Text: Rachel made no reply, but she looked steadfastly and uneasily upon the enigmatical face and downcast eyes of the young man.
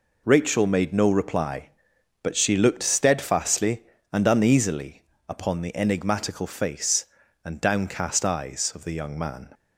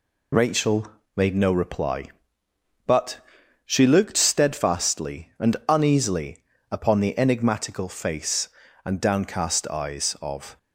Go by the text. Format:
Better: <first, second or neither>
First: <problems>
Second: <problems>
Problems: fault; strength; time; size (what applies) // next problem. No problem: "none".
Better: first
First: pauses between "uneasily" and "upon"; slight; at 5.0 s; 0.26 s long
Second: pauses between "Rachel" and "made"; slight; at 0.8 s; 0.28 s long // pauses between "but" and "she"; noticeable; at 3.1 s; 0.46 s long // pauses between "uneasily" and "upon"; slight; at 6.3 s; 0.34 s long // stops before "the young man"; at 10.5 s